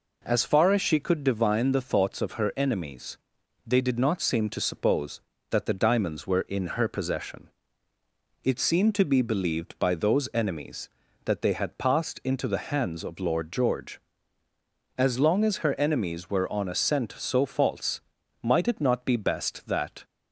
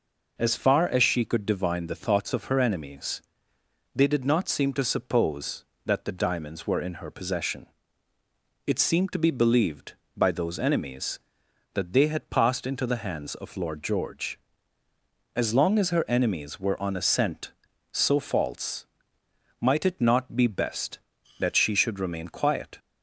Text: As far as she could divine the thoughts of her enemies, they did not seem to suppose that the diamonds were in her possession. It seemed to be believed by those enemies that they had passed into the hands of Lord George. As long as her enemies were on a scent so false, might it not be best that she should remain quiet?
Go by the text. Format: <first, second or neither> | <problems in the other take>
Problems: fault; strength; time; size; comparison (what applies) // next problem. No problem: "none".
second | stops before "she should remain quiet"; at 20.0 s